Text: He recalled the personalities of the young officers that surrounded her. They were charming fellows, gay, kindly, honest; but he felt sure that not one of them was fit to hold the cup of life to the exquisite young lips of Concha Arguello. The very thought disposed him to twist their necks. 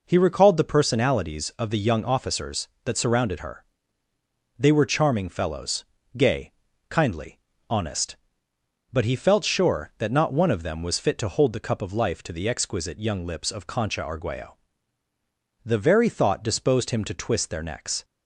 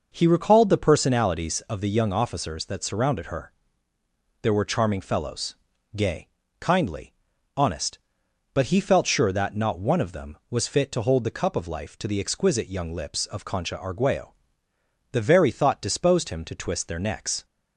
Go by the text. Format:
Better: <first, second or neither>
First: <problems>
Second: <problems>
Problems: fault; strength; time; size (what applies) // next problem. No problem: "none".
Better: first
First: none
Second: says "There" for "They"; at 4.4 s